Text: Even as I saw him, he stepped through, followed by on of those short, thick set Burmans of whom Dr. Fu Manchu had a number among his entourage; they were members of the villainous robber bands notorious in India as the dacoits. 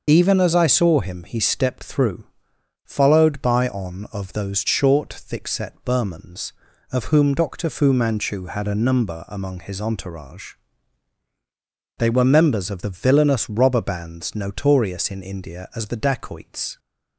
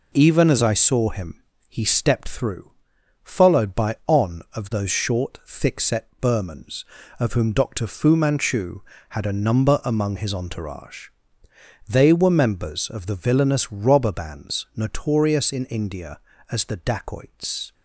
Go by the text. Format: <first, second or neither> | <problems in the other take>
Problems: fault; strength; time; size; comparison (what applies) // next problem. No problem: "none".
second | loses the start of "Even"; at 0.0 s; 40 ms